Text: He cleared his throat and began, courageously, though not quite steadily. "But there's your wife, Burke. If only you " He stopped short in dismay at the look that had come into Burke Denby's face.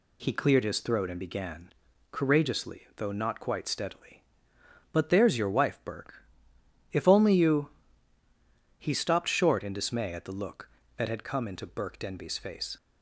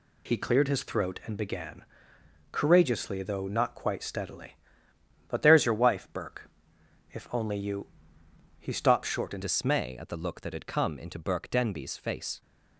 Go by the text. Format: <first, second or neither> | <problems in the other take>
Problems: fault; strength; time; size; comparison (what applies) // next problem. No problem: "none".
first | changes voice at "dismay"; from 9.4 s on; 3.0 s long